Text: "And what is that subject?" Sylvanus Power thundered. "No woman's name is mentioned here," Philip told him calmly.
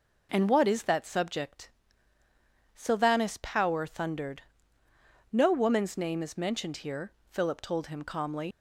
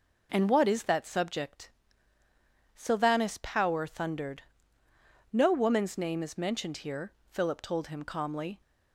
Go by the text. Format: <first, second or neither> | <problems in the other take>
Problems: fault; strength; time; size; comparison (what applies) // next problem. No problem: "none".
second | leaves "calmly" unfinished; at 8.5 s; 95 ms